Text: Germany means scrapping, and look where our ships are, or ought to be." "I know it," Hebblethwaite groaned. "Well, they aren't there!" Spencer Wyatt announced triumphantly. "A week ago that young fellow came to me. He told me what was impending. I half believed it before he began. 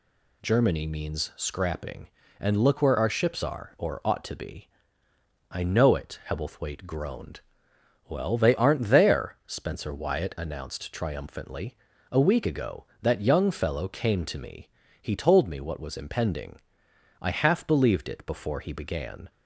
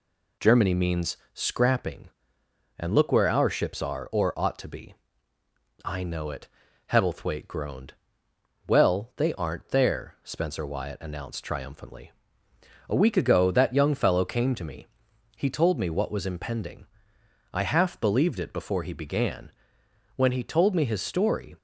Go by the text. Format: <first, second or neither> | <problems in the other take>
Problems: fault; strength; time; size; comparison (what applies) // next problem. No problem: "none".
first | pauses between "means" and "scrapping"; slight; at 1.1 s; 0.18 s long // goes on to say "When he told me his story"; from 20.1 s on; 1.4 s long